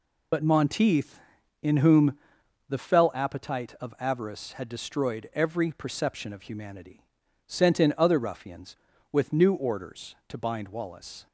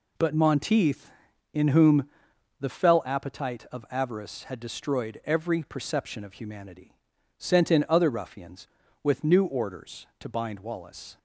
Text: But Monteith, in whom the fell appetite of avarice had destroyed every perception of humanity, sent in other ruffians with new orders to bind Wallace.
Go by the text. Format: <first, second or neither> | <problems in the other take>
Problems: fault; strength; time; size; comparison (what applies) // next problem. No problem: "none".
second | loses the start of "But"; at 0.3 s; 60 ms // pauses between "whom" and "the"; noticeable; at 2.1 s; 0.52 s long; noticeable in the second